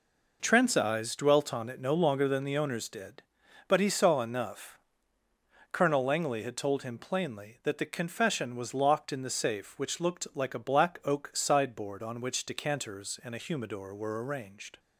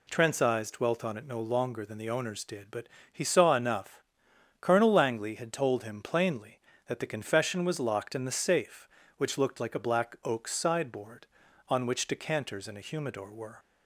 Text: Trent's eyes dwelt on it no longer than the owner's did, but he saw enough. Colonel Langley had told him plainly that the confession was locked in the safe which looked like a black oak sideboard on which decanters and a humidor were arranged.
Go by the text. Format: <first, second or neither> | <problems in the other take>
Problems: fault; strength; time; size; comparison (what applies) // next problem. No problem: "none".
first | pauses between "but" and "he"; slight; at 2.8 s; 0.24 s long // stops before "arranged"; at 13.5 s